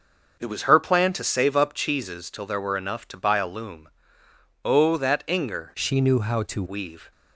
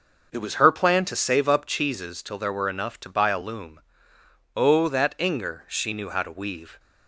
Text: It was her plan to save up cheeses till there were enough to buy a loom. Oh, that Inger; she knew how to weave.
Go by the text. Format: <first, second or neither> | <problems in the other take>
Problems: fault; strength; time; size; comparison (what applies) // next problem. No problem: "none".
second | starts louder than the rest; until 1.4 s; 6 dB; also in the second // changes voice from "she" to "to"; from 5.7 to 6.6 s; 0.9 s long